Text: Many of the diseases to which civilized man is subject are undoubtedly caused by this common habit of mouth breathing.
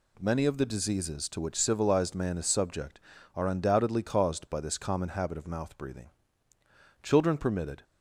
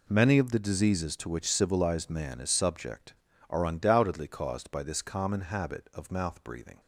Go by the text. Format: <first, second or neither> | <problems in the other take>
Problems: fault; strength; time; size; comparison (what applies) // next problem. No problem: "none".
second | goes on to say "Children permitted"; noticeable; from 7.0 s on; 0.80 s long